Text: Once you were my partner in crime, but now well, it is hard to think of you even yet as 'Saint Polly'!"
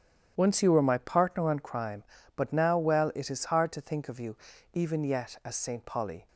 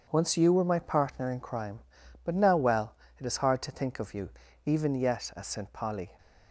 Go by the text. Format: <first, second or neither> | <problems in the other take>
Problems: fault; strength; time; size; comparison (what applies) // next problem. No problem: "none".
second | starts louder than the rest; strong; until 1.3 s; 10 dB // says "on" for "in"; at 1.4 s // pauses between "you" and "even"; at 4.3 s; 0.38 s long; slight in the second